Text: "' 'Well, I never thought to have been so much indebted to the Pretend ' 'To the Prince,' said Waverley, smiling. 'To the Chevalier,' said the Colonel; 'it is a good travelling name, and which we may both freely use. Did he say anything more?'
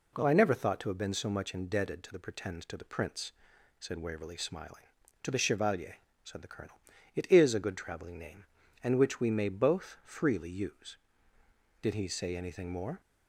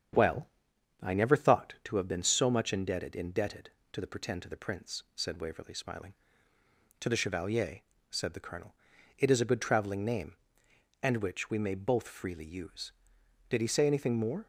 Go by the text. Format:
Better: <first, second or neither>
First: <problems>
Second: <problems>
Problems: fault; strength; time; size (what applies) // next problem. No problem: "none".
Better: first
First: none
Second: starts louder than the rest; strong; until 1.6 s; 8 dB // says "indebted" twice; at 3.1 s